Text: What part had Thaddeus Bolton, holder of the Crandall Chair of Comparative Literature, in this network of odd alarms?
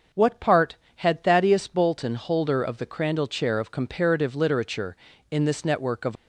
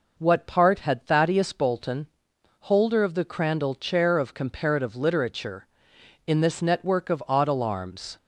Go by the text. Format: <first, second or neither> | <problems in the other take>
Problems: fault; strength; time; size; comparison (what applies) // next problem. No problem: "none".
second | starts louder than the rest; until 1.3 s; 6.5 dB // stops before "odd alarms"; at 6.1 s